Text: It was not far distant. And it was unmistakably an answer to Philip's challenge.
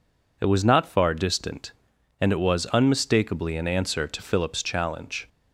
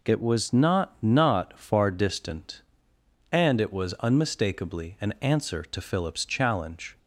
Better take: first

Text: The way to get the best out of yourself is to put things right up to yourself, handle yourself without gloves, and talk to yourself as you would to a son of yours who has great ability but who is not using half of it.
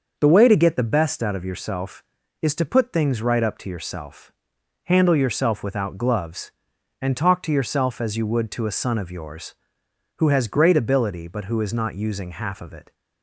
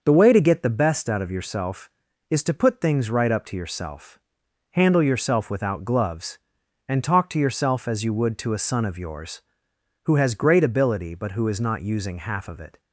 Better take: neither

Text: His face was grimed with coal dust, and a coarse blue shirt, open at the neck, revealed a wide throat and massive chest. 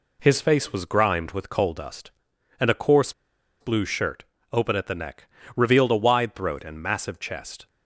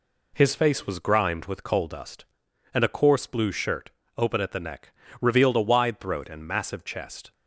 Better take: second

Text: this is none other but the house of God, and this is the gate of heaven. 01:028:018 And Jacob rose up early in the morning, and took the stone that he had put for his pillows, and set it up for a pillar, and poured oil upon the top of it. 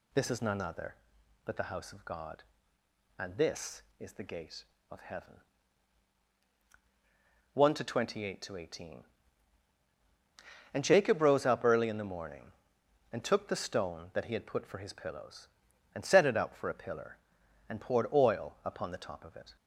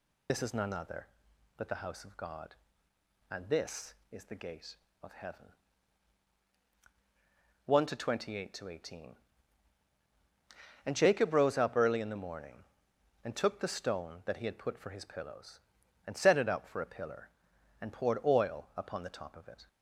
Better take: first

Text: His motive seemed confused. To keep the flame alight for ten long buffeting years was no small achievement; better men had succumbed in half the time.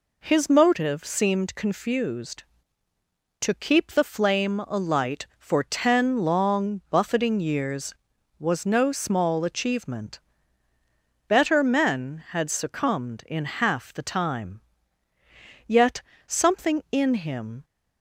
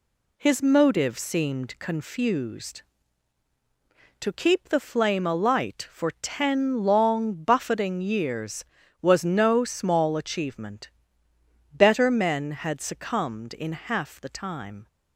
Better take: second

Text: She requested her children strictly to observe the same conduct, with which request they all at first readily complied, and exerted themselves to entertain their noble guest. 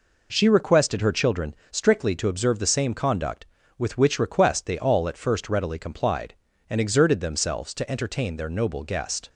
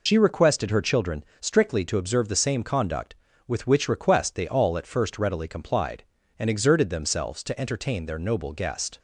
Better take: first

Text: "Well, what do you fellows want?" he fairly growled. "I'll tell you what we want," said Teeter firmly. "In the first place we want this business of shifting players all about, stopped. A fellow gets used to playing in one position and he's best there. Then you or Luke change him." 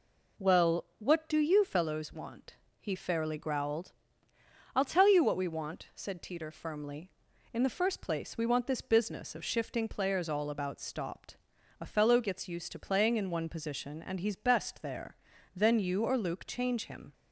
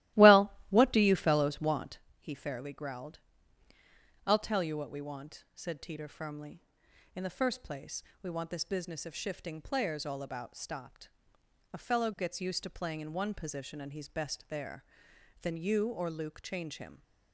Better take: first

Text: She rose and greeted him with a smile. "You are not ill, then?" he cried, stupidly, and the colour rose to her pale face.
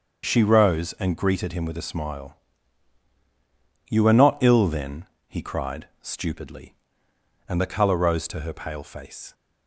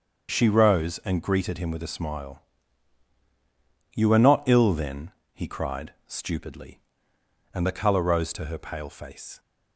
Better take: neither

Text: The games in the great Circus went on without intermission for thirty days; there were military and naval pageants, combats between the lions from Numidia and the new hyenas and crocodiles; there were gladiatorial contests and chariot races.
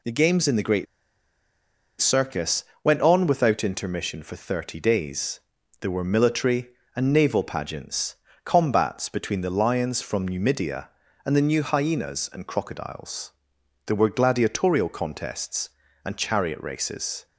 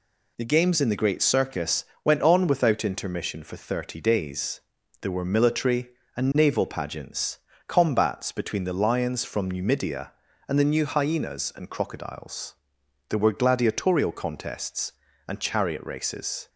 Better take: second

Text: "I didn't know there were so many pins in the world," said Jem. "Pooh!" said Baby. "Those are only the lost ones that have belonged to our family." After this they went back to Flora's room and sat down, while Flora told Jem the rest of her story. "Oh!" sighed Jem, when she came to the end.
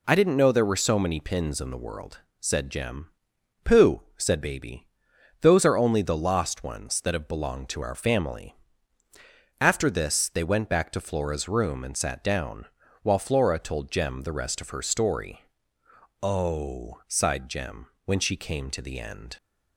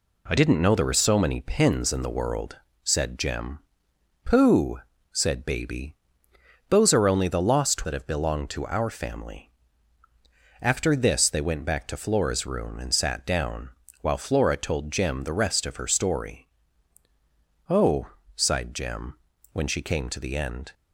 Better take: first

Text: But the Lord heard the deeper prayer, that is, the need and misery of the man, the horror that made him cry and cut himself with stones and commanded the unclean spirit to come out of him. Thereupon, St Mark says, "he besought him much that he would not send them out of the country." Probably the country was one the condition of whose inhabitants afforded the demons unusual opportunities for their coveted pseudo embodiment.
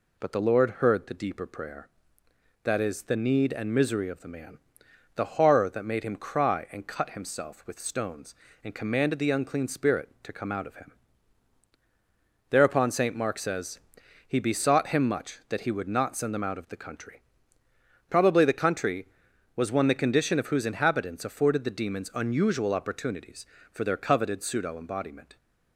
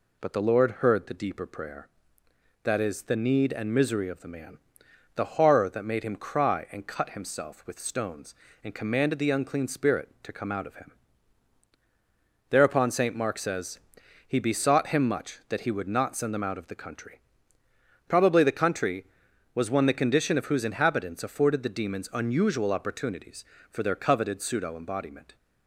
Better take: neither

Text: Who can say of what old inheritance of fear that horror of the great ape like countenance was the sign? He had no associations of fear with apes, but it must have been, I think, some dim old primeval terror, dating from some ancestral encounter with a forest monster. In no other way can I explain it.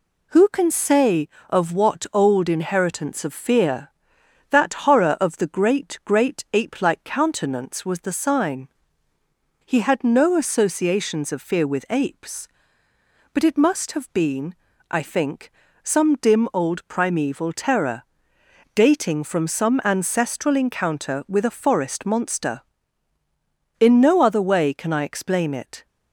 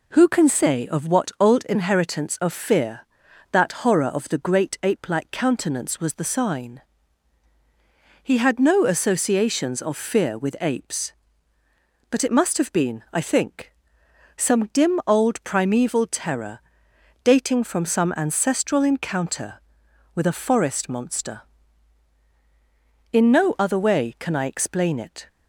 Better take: second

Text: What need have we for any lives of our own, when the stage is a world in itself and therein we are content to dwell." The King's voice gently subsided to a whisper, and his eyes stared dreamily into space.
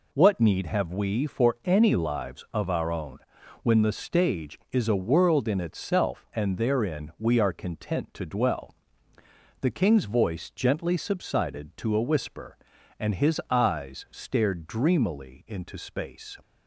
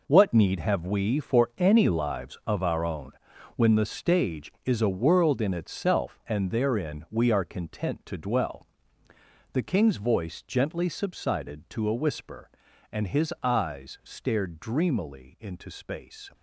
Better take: first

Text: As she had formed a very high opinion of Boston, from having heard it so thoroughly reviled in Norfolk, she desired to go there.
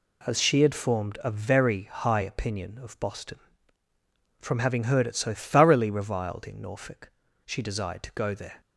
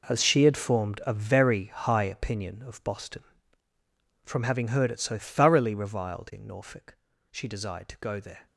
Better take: first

